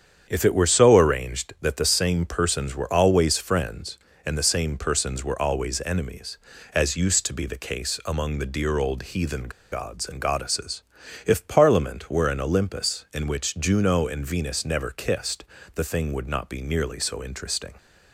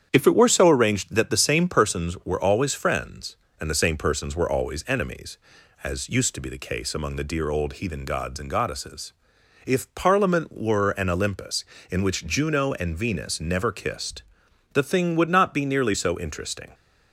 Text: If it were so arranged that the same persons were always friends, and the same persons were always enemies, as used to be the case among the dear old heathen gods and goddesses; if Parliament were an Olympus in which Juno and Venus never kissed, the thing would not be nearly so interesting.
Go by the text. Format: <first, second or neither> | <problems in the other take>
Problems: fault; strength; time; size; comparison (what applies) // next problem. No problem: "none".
second | starts louder than the rest; strong; until 1.3 s; 8 dB; strong in the second // pauses between "heathen" and "gods"; slight; at 9.4 s; 0.22 s long